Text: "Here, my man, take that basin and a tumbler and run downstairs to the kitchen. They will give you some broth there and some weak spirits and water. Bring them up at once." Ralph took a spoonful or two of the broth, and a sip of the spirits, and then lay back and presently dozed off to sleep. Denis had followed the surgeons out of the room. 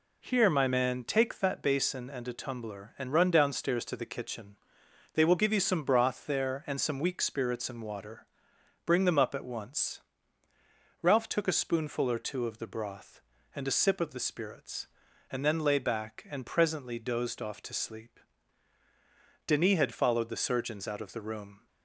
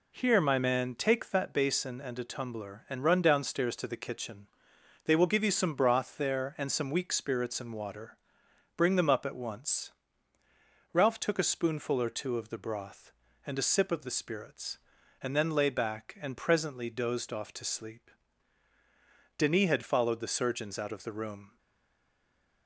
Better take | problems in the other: first | stays silent after the last word; from 21.5 s on; 1.1 s long

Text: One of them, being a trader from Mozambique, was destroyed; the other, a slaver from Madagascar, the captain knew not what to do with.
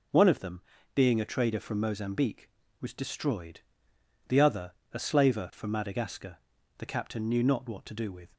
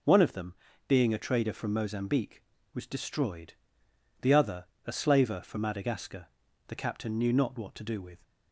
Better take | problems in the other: neither | none

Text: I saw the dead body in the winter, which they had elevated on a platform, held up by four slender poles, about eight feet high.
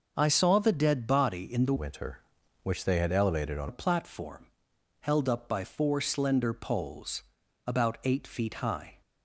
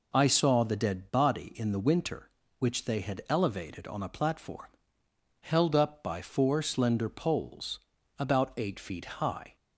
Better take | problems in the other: second | starts louder than the rest; noticeable; until 1.1 s; 6 dB // changes voice from "winter" to "on"; from 1.7 to 3.6 s; 1.9 s long

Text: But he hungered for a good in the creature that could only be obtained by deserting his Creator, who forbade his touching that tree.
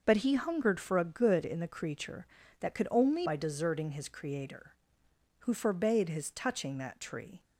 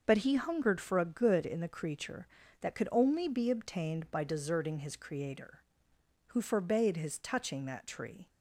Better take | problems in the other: second | starts louder than the rest; until 1.0 s; 6 dB; noticeable in the second // skips "be obtained"; at 3.2 s

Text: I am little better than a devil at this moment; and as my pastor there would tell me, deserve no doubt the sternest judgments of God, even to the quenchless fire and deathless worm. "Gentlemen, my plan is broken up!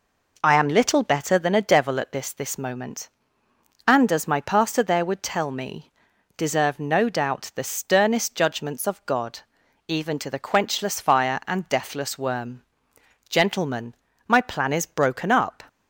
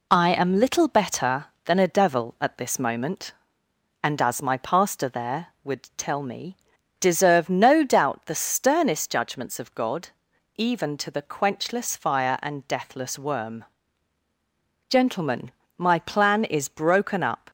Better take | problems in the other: second | says "this" twice; at 2.3 s

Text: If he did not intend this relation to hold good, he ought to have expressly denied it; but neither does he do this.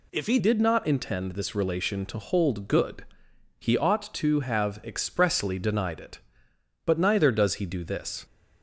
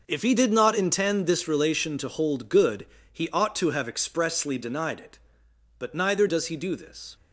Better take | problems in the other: second | changes voice at "did"; from 0.3 s on; 7.9 s long

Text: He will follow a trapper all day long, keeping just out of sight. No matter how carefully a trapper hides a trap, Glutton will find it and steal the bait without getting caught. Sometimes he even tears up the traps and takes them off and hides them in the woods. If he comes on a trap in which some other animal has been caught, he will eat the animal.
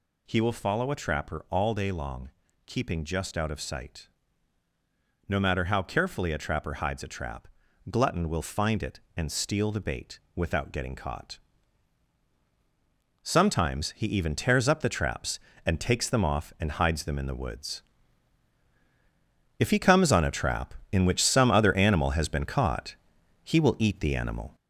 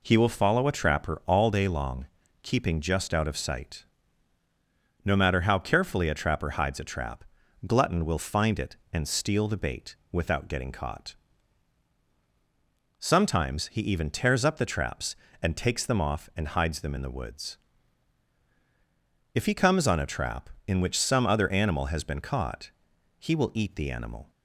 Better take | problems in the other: second | gets louder; noticeable; throughout; 4.5 dB // pauses between "bait" and "without"; slight; at 10.1 s; 0.16 s long; slight in the second

